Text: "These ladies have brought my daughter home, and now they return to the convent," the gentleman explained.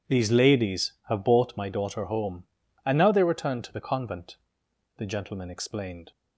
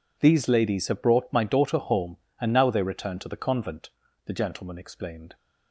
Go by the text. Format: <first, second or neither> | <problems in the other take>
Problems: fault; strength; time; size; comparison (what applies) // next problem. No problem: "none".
second | says "bought" for "brought"; at 1.2 s